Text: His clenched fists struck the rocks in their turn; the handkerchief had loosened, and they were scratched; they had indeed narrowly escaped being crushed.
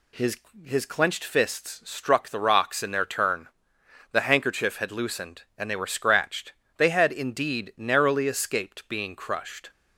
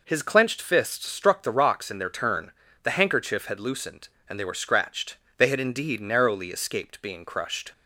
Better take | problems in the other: second | says "His" twice; at 0.6 s

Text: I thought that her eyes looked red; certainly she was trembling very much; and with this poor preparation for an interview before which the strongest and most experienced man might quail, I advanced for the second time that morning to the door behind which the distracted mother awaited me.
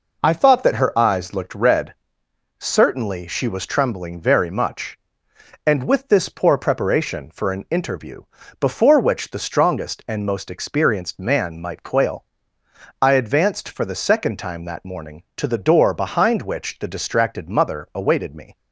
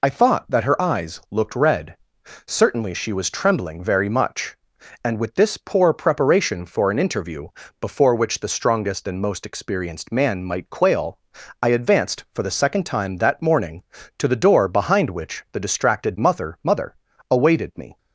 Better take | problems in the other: first | pauses between "interview" and "before"; slight; at 7.4 s; 0.32 s long; slight in the first // says "mother" twice; at 16.6 s

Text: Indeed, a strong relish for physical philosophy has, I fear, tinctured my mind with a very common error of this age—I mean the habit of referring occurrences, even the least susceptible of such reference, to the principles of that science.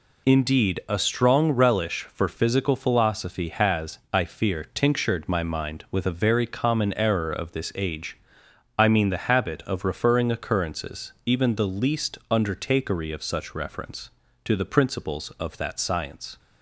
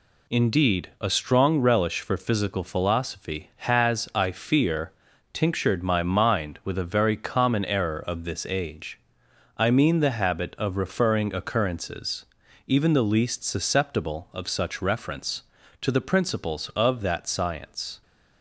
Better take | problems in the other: second | says "undertakery" for "susceptible"; at 12.3 s

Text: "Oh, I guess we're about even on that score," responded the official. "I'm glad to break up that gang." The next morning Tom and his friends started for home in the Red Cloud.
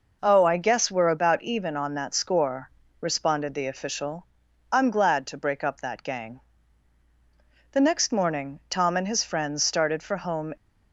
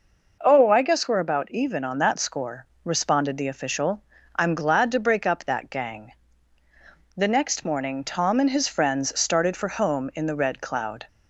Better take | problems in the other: second | stops before "in the Red Cloud"; at 10.5 s

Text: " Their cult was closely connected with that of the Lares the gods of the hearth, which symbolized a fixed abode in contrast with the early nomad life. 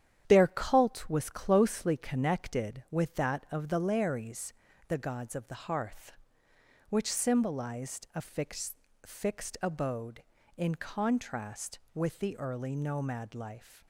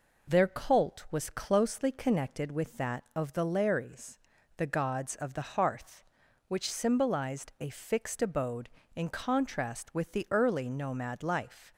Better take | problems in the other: second | starts louder than the rest; strong; until 1.2 s; 9.5 dB // pauses between "Lares" and "the"; slight; at 4.5 s; 0.34 s long; also in the second // says "fixed" twice; at 9.0 s

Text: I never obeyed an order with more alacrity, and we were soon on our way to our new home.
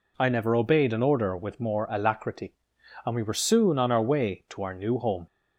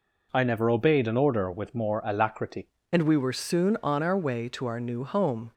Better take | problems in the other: first | changes voice at "and"; from 2.9 s on; 2.6 s long

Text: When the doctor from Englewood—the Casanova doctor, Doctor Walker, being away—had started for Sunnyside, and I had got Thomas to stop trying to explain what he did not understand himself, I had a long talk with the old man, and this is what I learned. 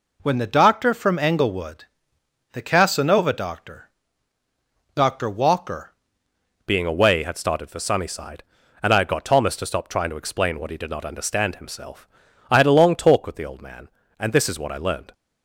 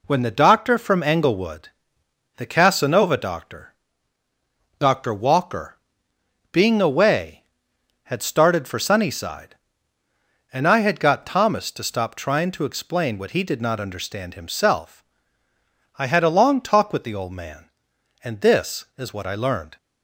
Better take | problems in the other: second | changes voice at "being"; from 6.6 s on; 8.5 s long

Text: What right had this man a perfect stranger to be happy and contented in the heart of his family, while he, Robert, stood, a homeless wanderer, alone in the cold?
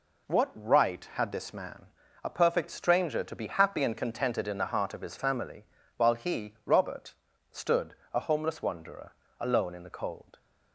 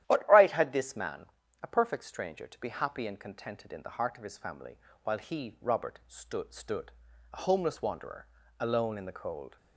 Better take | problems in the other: first | starts louder than the rest; strong; until 1.0 s; 12 dB // pauses between "man" and "a"; at 1.2 s; 0.38 s long; also in the first // says "stood" twice; at 6.5 s

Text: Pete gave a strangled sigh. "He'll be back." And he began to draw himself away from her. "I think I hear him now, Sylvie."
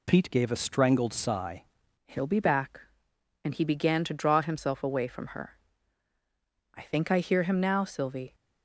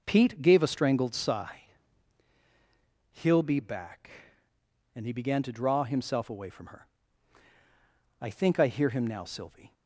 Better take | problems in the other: second | changes voice at "He'll"; from 2.0 s on; 6.3 s long

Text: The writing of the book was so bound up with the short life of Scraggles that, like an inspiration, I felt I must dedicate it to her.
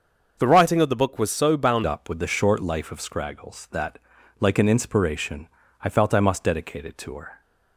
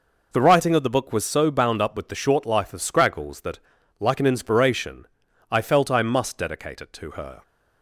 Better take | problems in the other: second | starts louder than the rest; until 1.4 s; 6.5 dB // changes voice at "up"; from 1.8 s on; 5.6 s long

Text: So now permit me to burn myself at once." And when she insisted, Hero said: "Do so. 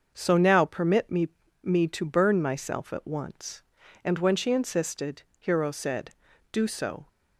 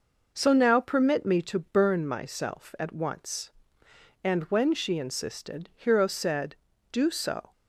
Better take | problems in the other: second | starts louder than the rest; until 1.1 s; 6.5 dB // says "me" twice; at 1.6 s

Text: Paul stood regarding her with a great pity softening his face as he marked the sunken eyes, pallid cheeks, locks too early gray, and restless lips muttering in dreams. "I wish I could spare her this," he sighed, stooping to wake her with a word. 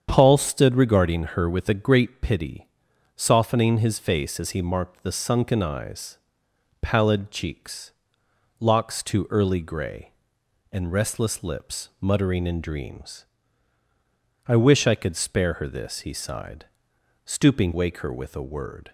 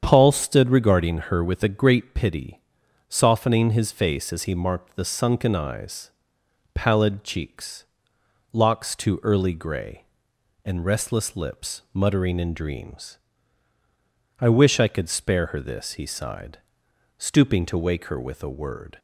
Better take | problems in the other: second | starts louder than the rest; strong; until 1.1 s; 8 dB; strong in the second // pauses between "regarding" and "her"; slight; at 1.2 s; 0.16 s long; slight in the second // pauses between "pity" and "softening"; noticeable; at 2.6 s; 0.50 s long; noticeable in the second // skips "to"; at 17.7 s

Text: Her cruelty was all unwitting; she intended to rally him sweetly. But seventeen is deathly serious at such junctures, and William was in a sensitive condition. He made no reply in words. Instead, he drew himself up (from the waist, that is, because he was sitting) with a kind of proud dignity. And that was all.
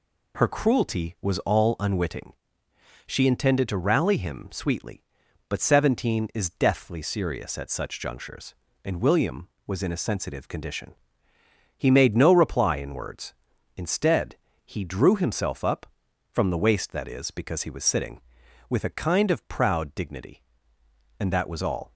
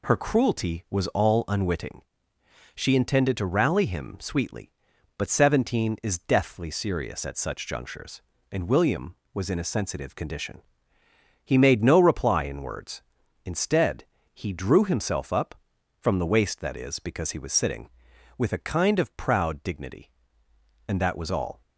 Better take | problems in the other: neither | none

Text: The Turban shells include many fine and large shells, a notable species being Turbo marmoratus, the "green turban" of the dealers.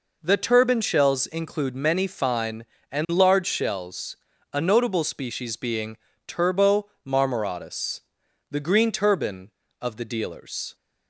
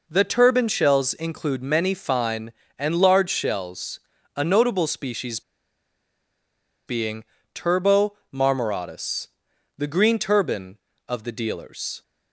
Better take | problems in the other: first | pauses between "species" and "being"; strong; at 5.4 s; 1.4 s long // pauses between "being" and "Turbo"; slight; at 7.2 s; 0.30 s long; slight in the first // pauses between "Turbo" and "marmoratus"; slight; at 8.1 s; 0.18 s long; slight in the first

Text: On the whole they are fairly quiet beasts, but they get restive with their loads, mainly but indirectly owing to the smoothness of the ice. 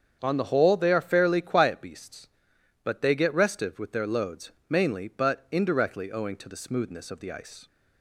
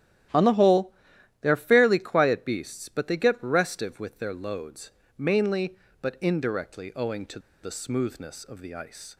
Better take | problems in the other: first | starts louder than the rest; strong; until 1.8 s; 12.5 dB; strong in the first // pauses between "whole" and "they"; noticeable; at 0.9 s; 0.50 s long // pauses between "to" and "the"; slight; at 7.3 s; 0.23 s long

